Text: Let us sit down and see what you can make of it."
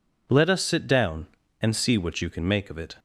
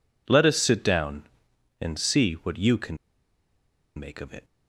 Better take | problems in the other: first | pauses between "can" and "make"; at 2.9 s; 1.0 s long

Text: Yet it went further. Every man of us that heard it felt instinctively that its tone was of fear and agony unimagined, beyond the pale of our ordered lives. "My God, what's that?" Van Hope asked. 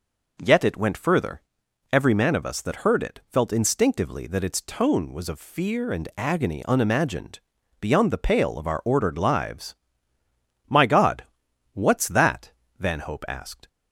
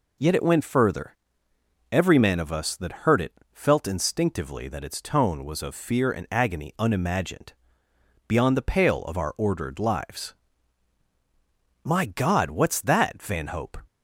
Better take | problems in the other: first | pauses between "it" and "felt"; slight; at 3.3 s; 0.20 s long // stops before "asked"; at 13.8 s

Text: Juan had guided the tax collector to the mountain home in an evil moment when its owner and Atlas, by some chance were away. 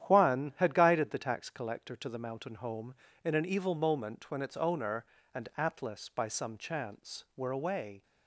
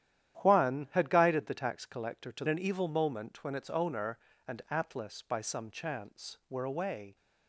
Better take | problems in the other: first | starts louder than the rest; strong; until 1.4 s; 11 dB; strong in the first // skips "the mountain home in"; at 2.4 s

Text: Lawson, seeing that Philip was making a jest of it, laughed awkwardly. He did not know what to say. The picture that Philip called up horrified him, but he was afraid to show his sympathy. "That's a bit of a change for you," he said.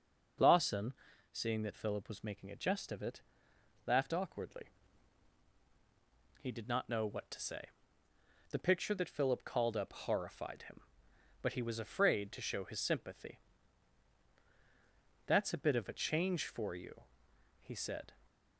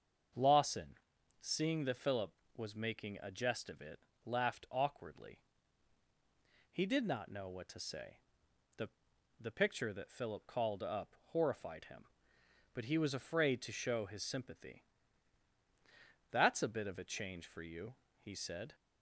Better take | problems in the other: first | starts louder than the rest; until 1.8 s; 6.5 dB // says "The" twice; at 9.3 s // pauses between "up" and "horrified"; slight; at 11.1 s; 0.16 s long

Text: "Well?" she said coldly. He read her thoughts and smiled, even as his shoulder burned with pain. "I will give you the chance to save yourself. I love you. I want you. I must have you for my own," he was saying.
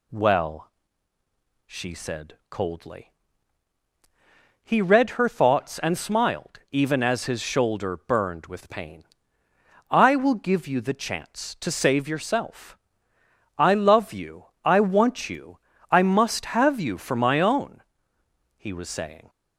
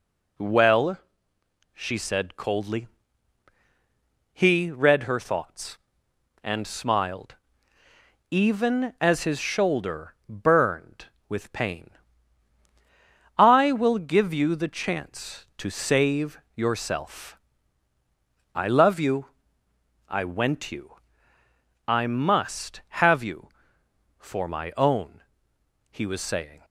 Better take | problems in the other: first | pauses between "save" and "yourself"; slight; at 16.3 s; 0.16 s long // says "went" for "want"; at 20.2 s

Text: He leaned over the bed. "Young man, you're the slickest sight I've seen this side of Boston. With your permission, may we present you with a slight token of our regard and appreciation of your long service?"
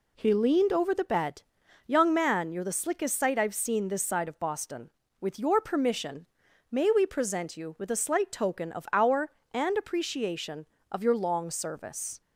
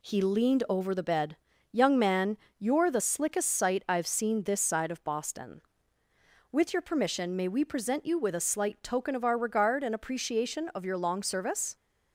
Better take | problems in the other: second | skips "regard"; at 9.4 s

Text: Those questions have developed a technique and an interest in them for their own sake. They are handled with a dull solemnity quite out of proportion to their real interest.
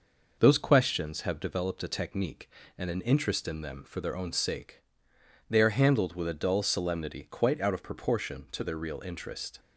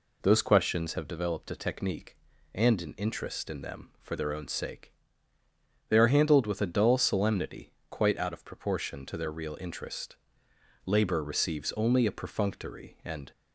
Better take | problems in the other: first | pauses between "solemnity" and "quite"; slight; at 7.7 s; 0.18 s long // goes on to say "Labor receives only a perfunctory and"; strong; from 10.8 s on; 2.4 s long

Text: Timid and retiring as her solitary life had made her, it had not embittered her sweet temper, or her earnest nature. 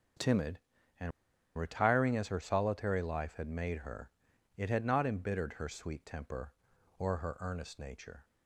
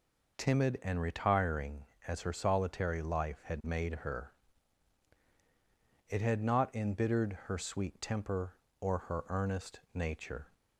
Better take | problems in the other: second | starts louder than the rest; until 2.0 s; 6.5 dB // pauses between "and" and "retiring"; noticeable; at 1.1 s; 0.47 s long

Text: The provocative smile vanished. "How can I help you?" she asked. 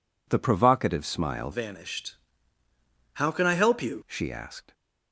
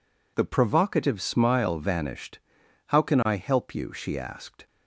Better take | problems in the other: second | changes voice from "vanished" to "you"; from 1.5 to 4.0 s; 2.5 s long

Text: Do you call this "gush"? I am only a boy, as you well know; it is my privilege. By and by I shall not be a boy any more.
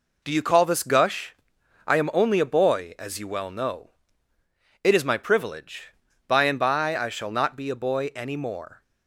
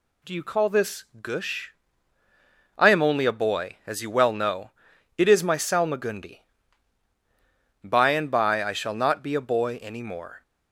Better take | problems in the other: first | pauses between "this" and "gush"; slight; at 1.0 s; 0.18 s long // says "salmagundi" for "privilege"; at 5.5 s

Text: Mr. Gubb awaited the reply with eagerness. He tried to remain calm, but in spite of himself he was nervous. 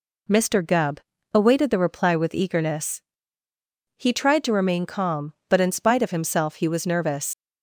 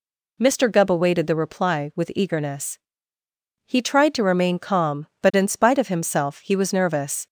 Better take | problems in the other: second | pauses between "Gubb" and "awaited"; slight; at 0.9 s; 0.36 s long // leaves "nervous" unfinished; at 7.3 s; 95 ms

